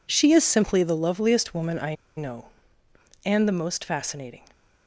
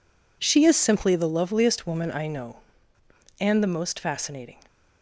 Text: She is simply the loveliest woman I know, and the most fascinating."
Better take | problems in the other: second | pauses between "I" and "know"; slight; at 1.9 s; 0.23 s long

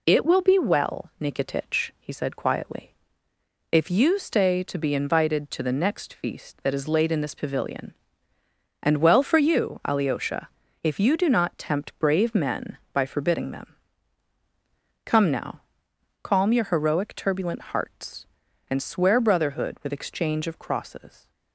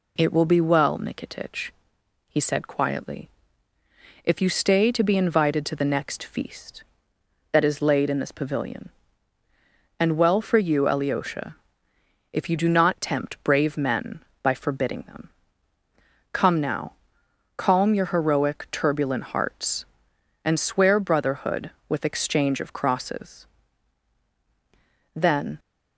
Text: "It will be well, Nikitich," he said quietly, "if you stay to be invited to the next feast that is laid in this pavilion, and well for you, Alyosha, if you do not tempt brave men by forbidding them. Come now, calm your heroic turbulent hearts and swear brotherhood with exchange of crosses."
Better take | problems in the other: first | goes on to say "Then"; slight; from 25.1 s on; 0.44 s long

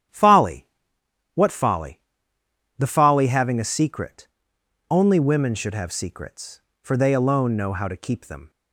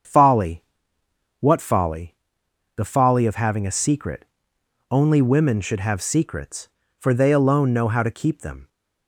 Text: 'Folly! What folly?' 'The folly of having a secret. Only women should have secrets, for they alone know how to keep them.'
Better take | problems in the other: second | starts louder than the rest; strong; until 1.7 s; 10.5 dB; strong in the second // skips "of"; at 3.2 s

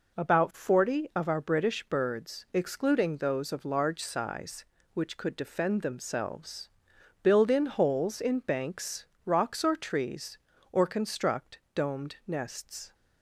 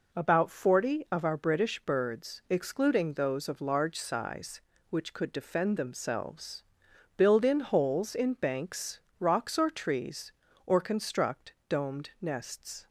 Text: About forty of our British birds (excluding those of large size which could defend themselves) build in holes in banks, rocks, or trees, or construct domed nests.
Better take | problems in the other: neither | pauses between "construct" and "domed"; slight; the same in both

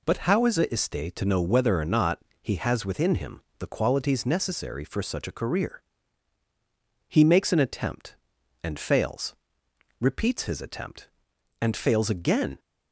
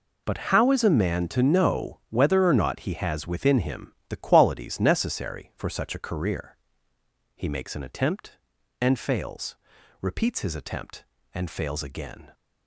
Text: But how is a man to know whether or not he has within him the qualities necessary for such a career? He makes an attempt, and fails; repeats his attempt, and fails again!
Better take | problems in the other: second | says "iste" for "man"; at 0.6 s // pauses between "not" and "he"; slight; at 2.1 s; 0.22 s long // pauses between "him" and "the"; slight; at 3.4 s; 0.18 s long

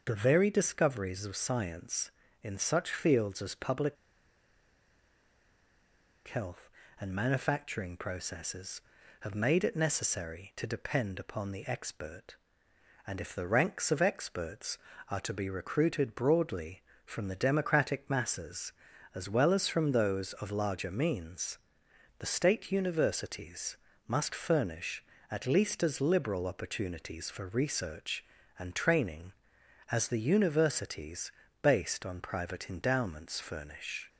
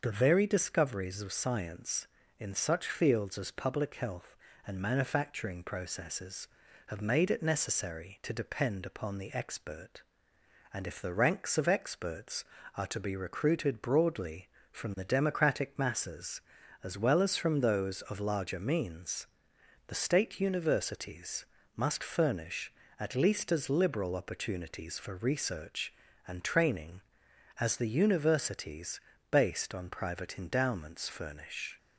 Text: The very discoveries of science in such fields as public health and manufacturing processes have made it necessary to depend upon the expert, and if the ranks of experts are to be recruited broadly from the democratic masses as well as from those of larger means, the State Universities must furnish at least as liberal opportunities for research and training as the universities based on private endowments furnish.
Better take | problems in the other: second | starts louder than the rest; noticeable; until 1.0 s; 6 dB; noticeable in the second // pauses between "public" and "health"; strong; at 3.9 s; 2.3 s long // pauses between "Universities" and "must"; slight; at 23.7 s; 0.30 s long; slight in the second // pauses between "universities" and "based"; slight; at 31.3 s; 0.30 s long; slight in the second

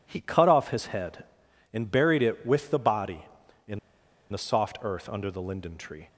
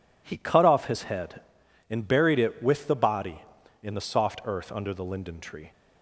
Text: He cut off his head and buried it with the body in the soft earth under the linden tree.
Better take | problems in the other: second | pauses between "in" and "the"; noticeable; at 3.7 s; 0.53 s long

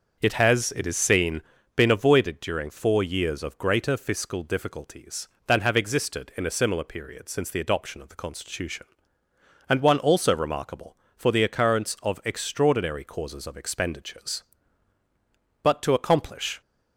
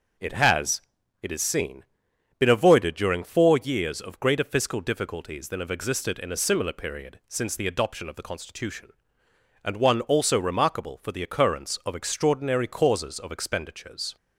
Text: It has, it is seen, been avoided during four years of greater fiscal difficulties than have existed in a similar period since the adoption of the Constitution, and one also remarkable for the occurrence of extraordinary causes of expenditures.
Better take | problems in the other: second | starts louder than the rest; until 1.2 s; 6.5 dB // goes on to say "But to accomplish"; noticeable; from 15.6 s on; 0.98 s long

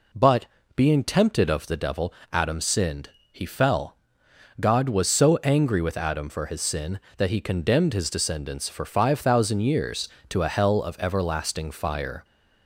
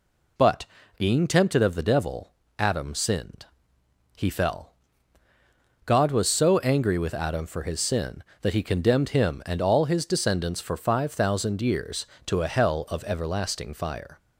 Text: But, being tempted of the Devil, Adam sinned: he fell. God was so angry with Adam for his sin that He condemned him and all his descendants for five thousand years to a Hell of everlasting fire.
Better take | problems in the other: second | skips "him and all"; at 7.9 s

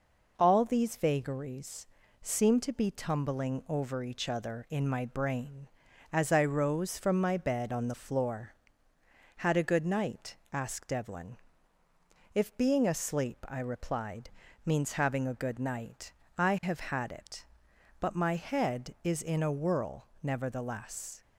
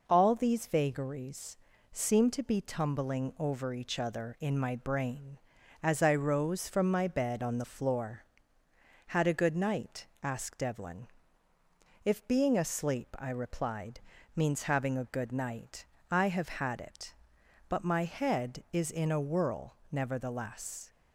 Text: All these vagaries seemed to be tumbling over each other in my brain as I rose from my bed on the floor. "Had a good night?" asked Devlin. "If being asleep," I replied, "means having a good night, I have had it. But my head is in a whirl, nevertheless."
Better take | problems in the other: neither | pauses between "vagaries" and "seemed"; slight; the same in both

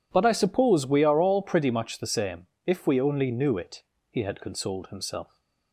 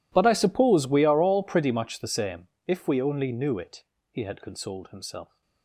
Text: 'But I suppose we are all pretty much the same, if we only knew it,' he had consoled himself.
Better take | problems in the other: first | gets quieter; strong; throughout; 24.5 dB

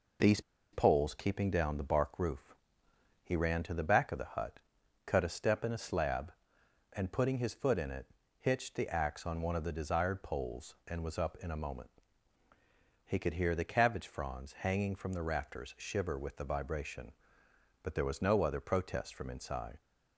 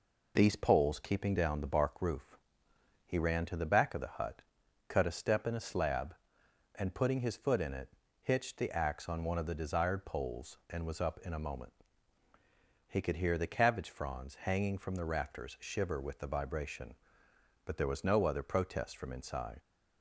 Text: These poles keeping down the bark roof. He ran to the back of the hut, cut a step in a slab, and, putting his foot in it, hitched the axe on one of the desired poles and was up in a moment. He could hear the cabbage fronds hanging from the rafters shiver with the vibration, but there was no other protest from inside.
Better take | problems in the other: second | pauses between "These" and "poles"; slight; at 0.4 s; 0.31 s long

